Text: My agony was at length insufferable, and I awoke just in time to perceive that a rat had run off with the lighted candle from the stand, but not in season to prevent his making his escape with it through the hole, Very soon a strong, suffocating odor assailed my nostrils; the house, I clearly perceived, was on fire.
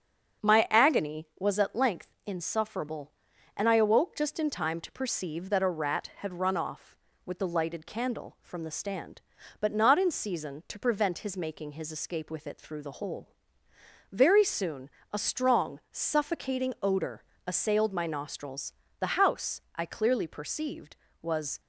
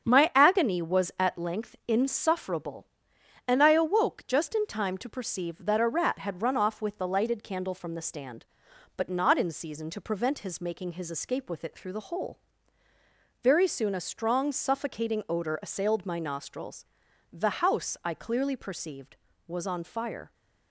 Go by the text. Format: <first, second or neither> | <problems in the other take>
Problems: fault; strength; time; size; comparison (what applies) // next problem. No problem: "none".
second | starts louder than the rest; until 1.5 s; 7 dB; strong in the second // pauses between "soon" and "a"; slight; at 14.8 s; 0.22 s long // pauses between "odor" and "assailed"; slight; at 17.2 s; 0.24 s long // stops before "on fire"; at 21.5 s